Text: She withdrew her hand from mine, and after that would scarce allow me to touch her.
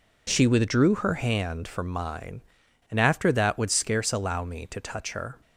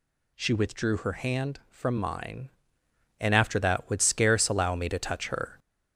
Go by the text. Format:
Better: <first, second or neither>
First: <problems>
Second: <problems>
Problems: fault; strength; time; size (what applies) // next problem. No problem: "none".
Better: first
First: none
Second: gets louder; throughout; 3.5 dB